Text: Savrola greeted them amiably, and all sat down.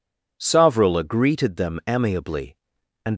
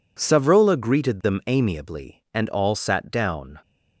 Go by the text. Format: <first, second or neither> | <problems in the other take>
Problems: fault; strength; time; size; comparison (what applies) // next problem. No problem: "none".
second | stops before "all sat down"; at 3.1 s